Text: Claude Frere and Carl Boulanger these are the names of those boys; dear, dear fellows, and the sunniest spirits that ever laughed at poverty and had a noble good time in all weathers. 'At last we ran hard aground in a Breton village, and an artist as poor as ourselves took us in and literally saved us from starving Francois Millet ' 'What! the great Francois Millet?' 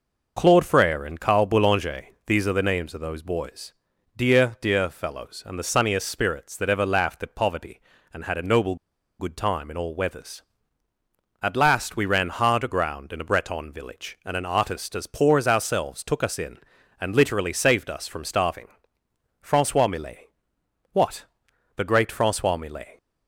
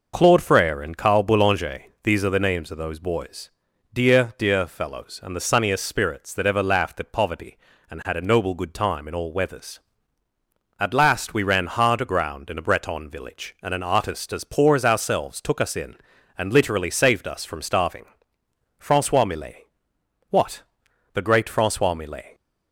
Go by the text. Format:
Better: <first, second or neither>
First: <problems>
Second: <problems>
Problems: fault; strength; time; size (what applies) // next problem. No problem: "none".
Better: second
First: pauses between "Boulanger" and "these"; slight; at 2.0 s; 0.18 s long // pauses between "noble" and "good"; at 8.7 s; 0.43 s long // pauses between "starving" and "Francois"; noticeable; at 18.6 s; 0.72 s long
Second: pauses between "Boulanger" and "these"; slight; at 1.8 s; 0.18 s long // pauses between "starving" and "Francois"; noticeable; at 18.0 s; 0.72 s long